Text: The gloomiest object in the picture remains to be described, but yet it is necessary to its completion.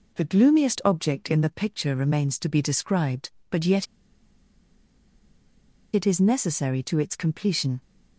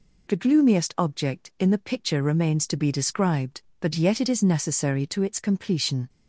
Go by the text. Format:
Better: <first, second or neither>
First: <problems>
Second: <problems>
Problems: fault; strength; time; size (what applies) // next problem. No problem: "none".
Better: second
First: pauses between "yet" and "it"; strong; at 3.8 s; 2.0 s long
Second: none